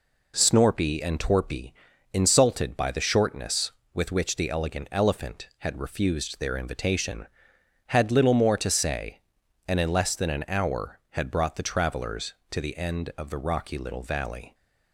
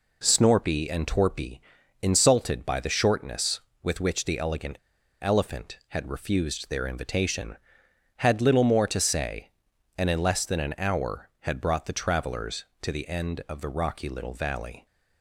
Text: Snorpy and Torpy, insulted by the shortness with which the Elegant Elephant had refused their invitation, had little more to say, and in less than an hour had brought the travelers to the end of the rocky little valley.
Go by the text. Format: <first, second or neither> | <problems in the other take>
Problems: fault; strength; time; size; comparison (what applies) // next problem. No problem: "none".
first | pauses between "Elegant" and "Elephant"; at 4.7 s; 0.45 s long